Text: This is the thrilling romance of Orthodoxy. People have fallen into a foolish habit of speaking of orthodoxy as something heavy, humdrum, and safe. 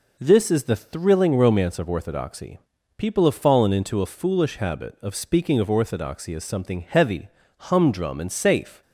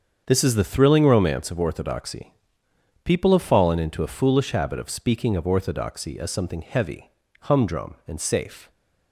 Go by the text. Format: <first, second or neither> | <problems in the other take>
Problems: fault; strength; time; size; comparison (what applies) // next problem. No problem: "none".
first | gets quieter; strong; throughout; 11 dB